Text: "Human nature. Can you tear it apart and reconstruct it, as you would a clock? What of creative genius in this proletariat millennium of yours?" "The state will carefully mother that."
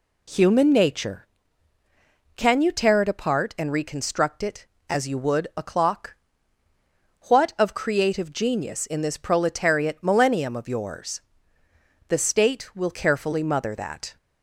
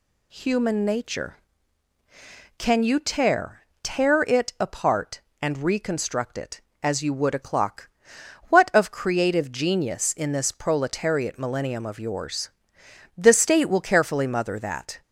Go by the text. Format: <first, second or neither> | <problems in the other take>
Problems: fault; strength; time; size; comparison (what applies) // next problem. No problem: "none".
first | says "tear" twice; at 3.8 s